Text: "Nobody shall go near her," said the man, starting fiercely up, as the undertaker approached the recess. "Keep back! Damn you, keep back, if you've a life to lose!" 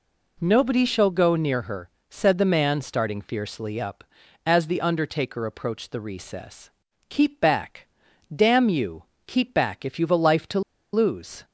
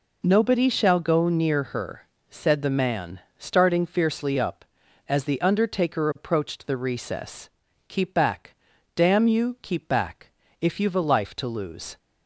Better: second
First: pauses between "to" and "lose"; slight; at 10.6 s; 0.32 s long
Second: none

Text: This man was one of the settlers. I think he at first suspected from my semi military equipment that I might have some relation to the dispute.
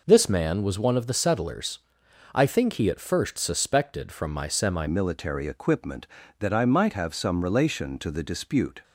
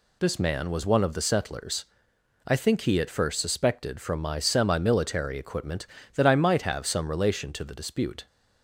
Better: second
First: changes voice at "military"; from 4.8 s on; 4.0 s long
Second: none

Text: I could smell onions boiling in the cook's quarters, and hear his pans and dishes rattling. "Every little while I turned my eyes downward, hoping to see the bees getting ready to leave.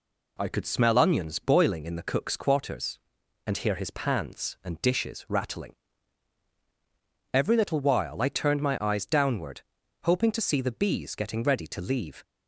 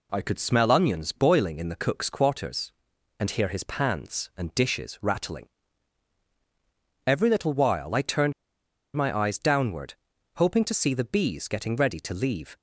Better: first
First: none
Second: pauses between "turned" and "my"; noticeable; at 8.3 s; 0.63 s long

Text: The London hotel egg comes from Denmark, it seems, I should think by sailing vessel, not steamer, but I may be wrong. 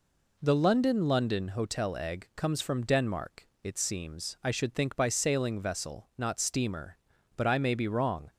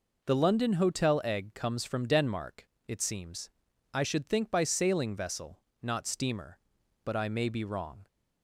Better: second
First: says "London" twice; at 1.0 s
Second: none

